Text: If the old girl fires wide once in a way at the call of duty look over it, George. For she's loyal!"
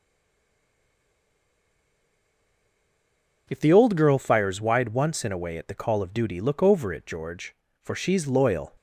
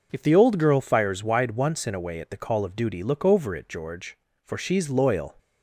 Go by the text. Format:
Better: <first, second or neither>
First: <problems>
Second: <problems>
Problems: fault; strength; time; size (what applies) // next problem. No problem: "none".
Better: second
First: stays silent before the first word; strong; until 3.4 s; 3.4 s long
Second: none